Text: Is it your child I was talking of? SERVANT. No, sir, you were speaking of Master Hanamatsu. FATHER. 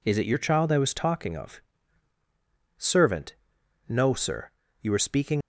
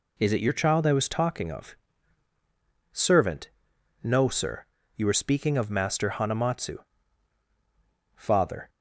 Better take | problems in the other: second | stops before "of Master Hanamatsu FATHER"; at 5.4 s

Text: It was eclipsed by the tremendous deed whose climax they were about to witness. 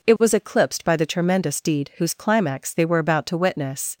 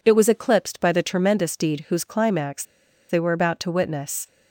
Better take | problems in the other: first | pauses between "climax" and "they"; noticeable; at 2.6 s; 0.46 s long

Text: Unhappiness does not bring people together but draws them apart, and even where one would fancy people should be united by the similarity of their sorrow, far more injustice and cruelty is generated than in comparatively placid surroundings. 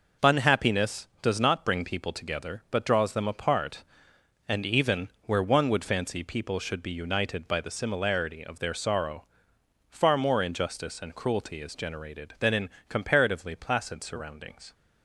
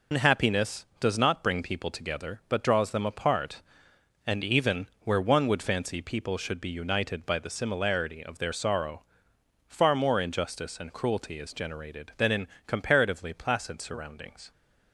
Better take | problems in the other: first | loses the start of "Unhappiness"; at 0.1 s; 125 ms // pauses between "even" and "where"; slight; at 4.8 s; 0.20 s long; slight in the first // pauses between "in" and "comparatively"; slight; at 12.4 s; 0.22 s long; slight in the first

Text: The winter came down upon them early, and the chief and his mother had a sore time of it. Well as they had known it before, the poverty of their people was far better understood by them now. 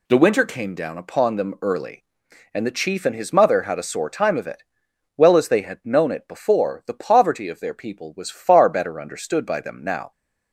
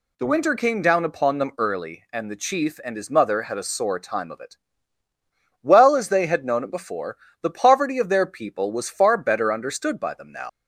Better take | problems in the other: first | leaves "now" unfinished; at 10.4 s; 110 ms

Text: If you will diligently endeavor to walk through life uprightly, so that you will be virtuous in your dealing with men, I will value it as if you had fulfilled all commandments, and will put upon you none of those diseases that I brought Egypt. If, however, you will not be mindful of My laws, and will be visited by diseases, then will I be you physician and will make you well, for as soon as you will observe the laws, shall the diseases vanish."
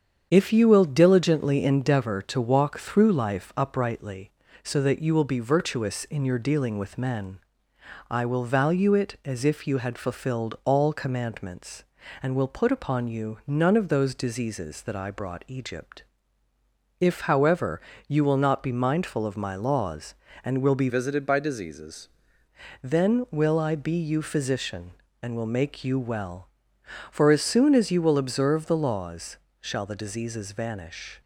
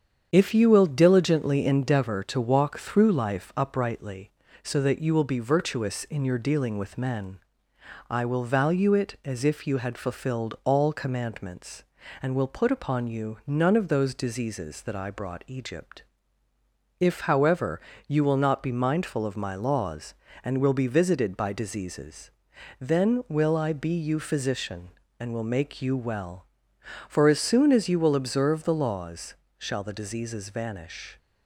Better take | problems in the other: second | starts louder than the rest; strong; until 1.3 s; 7.5 dB; strong in the second // changes voice from "visited" to "diseases"; from 20.8 to 22.0 s; 1.2 s long

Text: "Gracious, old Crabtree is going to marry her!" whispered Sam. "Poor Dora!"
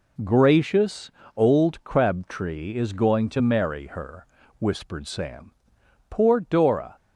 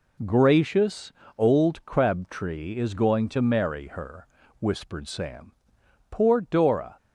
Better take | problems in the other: neither | none

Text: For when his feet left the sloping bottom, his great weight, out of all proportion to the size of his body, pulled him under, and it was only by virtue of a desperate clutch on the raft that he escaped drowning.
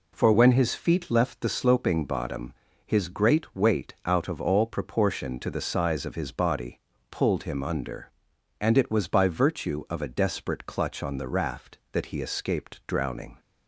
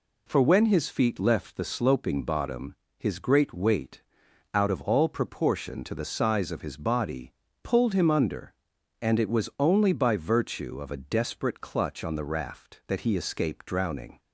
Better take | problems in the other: second | skips "only"; at 9.0 s

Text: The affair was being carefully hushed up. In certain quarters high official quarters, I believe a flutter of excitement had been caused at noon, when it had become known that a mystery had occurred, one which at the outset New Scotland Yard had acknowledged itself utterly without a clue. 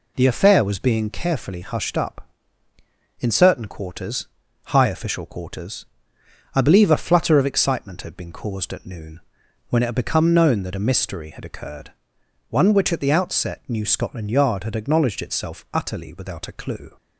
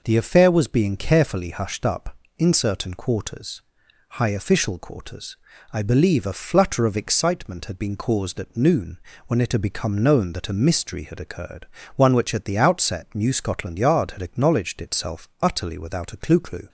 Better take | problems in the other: first | pauses between "quarters" and "high"; noticeable; at 3.6 s; 0.50 s long; also in the first // says "clue" twice; at 16.4 s

